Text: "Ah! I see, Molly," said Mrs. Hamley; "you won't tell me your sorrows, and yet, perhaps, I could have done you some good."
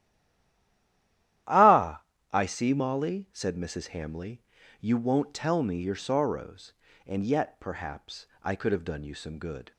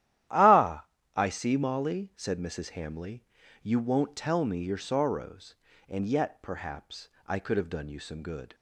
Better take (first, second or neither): second